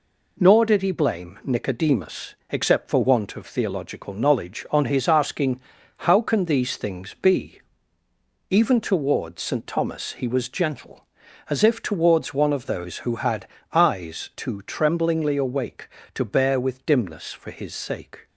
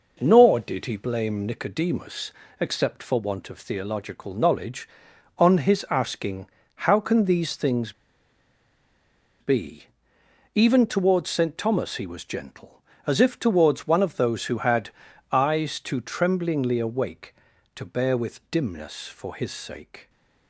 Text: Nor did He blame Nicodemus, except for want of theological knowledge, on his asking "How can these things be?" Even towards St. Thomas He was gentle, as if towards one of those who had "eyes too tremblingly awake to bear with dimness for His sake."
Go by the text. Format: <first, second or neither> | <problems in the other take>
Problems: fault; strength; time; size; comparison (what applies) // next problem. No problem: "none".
first | pauses between "asking" and "How"; at 6.4 s; 0.40 s long; noticeable in the first // pauses between "things" and "be"; strong; at 7.9 s; 1.4 s long // pauses between "had" and "eyes"; at 14.8 s; 0.42 s long; slight in the first